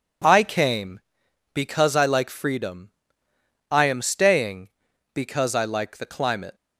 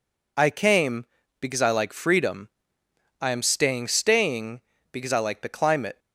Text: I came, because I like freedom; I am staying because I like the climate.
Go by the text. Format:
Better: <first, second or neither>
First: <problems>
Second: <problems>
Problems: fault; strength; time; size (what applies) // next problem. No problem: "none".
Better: first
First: none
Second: says "staying" twice; at 3.8 s